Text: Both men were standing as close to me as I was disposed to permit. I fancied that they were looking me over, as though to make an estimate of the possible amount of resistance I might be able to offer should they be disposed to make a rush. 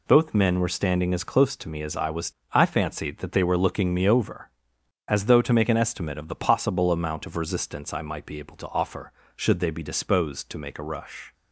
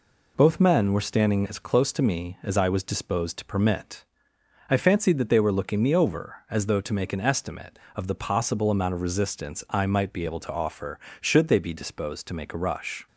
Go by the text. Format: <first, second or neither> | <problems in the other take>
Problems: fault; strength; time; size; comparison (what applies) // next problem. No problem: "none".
second | skips "disposed to permit"; at 2.4 s